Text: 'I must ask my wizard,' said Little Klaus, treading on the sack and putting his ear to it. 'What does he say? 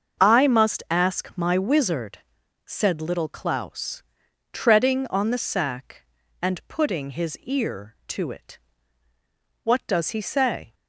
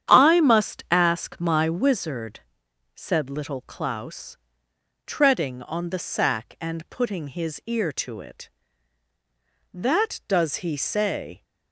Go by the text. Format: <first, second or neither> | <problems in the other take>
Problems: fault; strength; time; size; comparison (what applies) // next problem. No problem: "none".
first | starts louder than the rest; strong; until 1.1 s; 9.5 dB; also in the first // says "That" for "What"; at 9.7 s